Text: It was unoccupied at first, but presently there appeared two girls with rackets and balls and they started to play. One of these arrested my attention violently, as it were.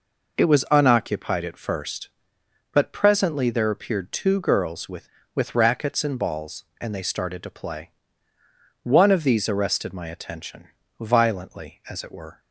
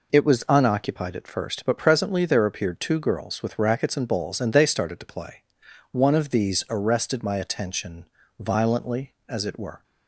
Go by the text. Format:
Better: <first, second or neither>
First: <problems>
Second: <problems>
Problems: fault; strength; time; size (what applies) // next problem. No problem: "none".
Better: second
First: says "with" twice; at 5.3 s // pauses between "attention" and "violently"; slight; at 10.6 s; 0.30 s long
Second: pauses between "attention" and "violently"; slight; at 8.0 s; 0.32 s long